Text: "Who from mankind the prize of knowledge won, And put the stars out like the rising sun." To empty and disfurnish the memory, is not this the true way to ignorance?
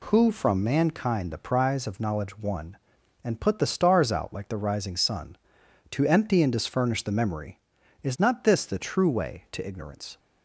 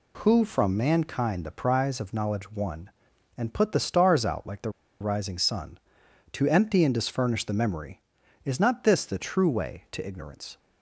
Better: first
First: none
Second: pauses between "the" and "rising"; slight; at 4.6 s; 0.30 s long

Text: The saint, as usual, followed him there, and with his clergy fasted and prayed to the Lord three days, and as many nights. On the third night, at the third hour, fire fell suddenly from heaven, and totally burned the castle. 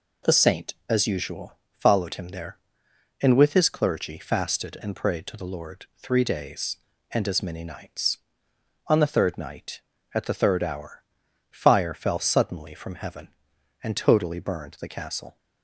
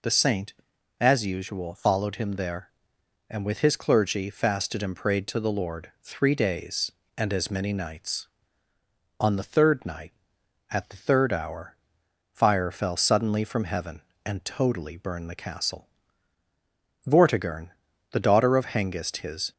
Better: first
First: none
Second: goes on to say "Vortigern the daughter of Hengist his"; strong; from 17.0 s on; 2.4 s long

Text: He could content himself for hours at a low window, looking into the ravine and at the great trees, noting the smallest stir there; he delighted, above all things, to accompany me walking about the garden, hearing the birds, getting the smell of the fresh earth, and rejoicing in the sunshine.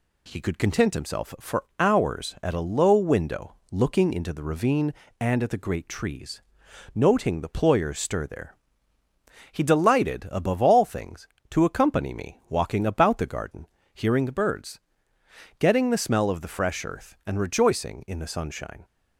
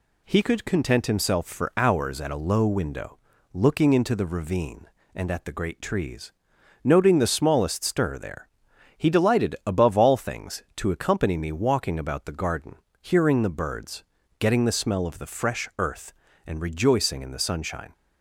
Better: second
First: pauses between "for" and "hours"; slight; at 1.6 s; 0.16 s long // says "ployers" for "smallest"; at 7.5 s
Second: none

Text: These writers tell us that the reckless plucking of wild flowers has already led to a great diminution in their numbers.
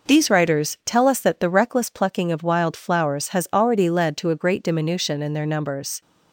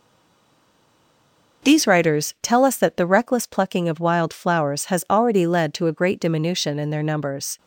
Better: first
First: none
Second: stays silent before the first word; noticeable; until 1.6 s; 1.6 s long

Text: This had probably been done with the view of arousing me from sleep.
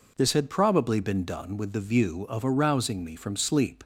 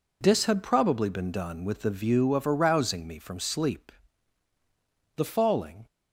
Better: first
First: none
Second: goes on to say "The falling"; noticeable; from 5.1 s on; 0.70 s long

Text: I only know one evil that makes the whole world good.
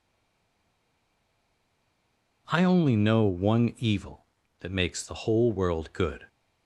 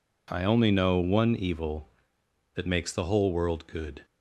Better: second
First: stays silent before the first word; until 2.4 s; 2.4 s long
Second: none

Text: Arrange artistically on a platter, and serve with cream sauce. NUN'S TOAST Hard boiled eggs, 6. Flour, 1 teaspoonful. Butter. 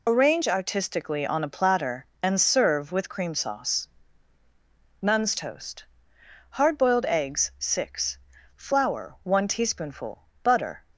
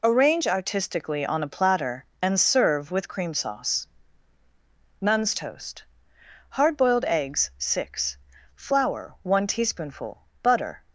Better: second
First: loses the start of "Arrange"; at 0.0 s; 35 ms // pauses between "TOAST" and "Hard"; noticeable; at 5.8 s; 0.68 s long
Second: pauses between "TOAST" and "Hard"; noticeable; at 5.8 s; 0.68 s long

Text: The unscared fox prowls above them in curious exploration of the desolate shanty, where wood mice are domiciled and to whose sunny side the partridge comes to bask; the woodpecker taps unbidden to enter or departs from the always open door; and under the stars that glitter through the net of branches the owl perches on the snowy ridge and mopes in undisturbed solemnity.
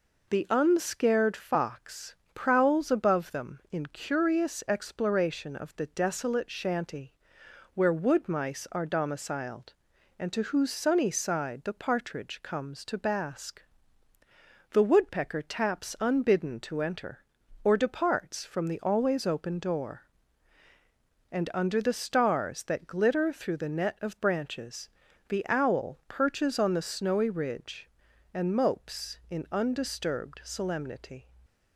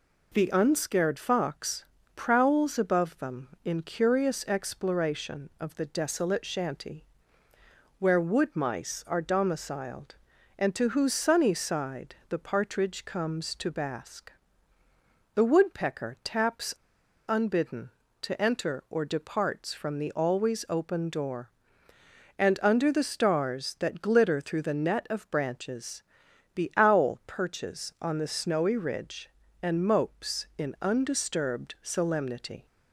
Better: first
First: pauses between "fox" and "prowls"; slight; at 2.1 s; 0.18 s long // pauses between "branches" and "the"; at 24.8 s; 0.40 s long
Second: pauses between "fox" and "prowls"; slight; at 1.8 s; 0.30 s long // pauses between "side" and "the"; slight; at 12.1 s; 0.16 s long // pauses between "taps" and "unbidden"; noticeable; at 16.7 s; 0.56 s long // pauses between "branches" and "the"; noticeable; at 26.0 s; 0.52 s long

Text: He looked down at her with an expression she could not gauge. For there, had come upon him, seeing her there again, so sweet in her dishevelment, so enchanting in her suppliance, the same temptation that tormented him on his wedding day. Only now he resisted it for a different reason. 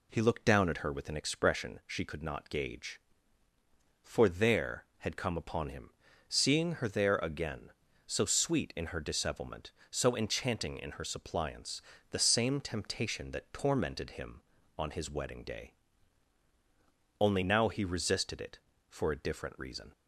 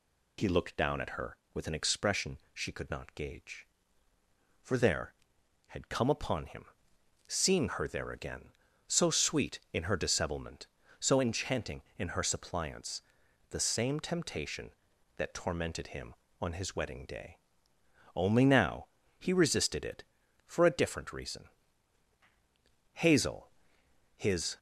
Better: first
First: none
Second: pauses between "expression" and "she"; slight; at 2.3 s; 0.16 s long // pauses between "now" and "he"; slight; at 18.8 s; 0.32 s long // goes on to say "Hazel his"; from 22.9 s on; 1.6 s long

